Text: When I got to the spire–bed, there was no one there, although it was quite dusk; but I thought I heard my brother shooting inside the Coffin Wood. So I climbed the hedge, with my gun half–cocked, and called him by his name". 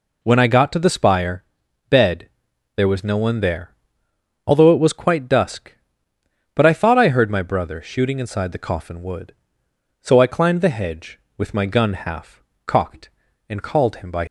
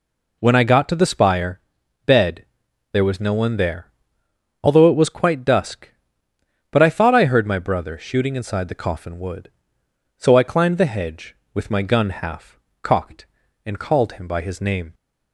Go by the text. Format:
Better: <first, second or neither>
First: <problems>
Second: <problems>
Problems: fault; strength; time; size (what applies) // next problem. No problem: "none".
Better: second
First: stops before "his name"; at 14.2 s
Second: none